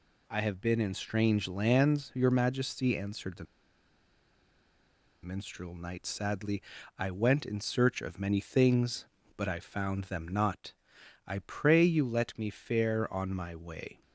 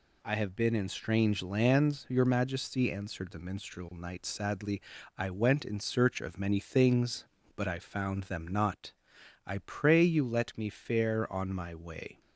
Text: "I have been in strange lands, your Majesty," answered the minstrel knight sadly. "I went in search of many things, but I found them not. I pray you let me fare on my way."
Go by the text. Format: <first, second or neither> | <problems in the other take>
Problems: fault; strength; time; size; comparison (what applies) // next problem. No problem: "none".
second | pauses between "the" and "minstrel"; strong; at 3.4 s; 1.7 s long